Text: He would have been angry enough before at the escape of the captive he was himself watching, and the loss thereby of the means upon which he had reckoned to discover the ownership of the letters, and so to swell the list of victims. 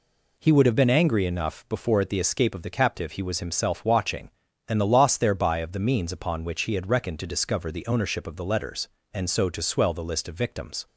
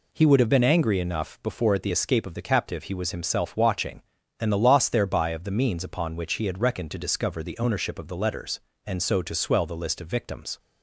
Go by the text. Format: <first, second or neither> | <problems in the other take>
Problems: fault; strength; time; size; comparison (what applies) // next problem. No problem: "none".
neither | none